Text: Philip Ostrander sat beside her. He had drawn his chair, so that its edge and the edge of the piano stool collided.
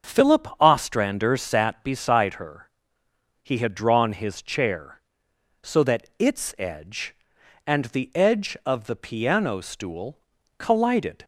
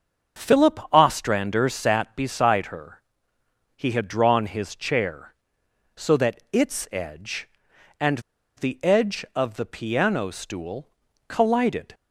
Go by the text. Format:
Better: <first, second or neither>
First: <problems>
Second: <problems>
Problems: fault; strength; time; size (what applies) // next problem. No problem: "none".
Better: first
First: starts louder than the rest; until 1.1 s; 6.5 dB // pauses between "stool" and "collided"; at 10.1 s; 0.40 s long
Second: starts louder than the rest; until 1.5 s; 7 dB // pauses between "and" and "the"; at 8.1 s; 0.37 s long // pauses between "stool" and "collided"; at 10.8 s; 0.40 s long